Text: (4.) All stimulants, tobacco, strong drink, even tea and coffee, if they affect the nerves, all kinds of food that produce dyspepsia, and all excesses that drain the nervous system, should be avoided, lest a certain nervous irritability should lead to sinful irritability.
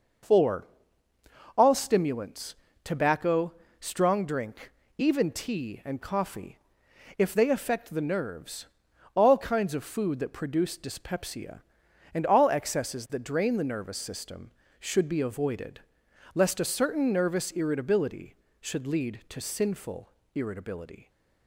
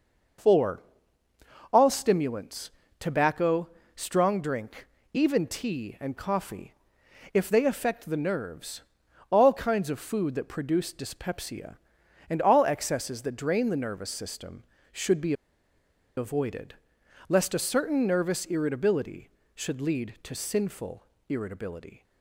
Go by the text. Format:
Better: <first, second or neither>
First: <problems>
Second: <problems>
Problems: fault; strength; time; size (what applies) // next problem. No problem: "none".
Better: first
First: pauses between "sinful" and "irritability"; slight; at 20.1 s; 0.24 s long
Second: pauses between "be" and "avoided"; noticeable; at 15.3 s; 0.83 s long // pauses between "sinful" and "irritability"; slight; at 21.0 s; 0.24 s long